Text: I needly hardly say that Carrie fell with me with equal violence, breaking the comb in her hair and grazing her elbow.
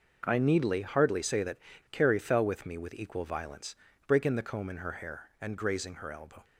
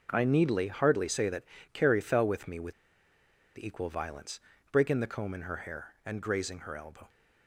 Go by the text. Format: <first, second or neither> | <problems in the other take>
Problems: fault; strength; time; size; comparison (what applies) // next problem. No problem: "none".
first | pauses between "that" and "Carrie"; slight; at 1.4 s; 0.28 s long; slight in the first // pauses between "with" and "equal"; noticeable; at 2.7 s; 0.85 s long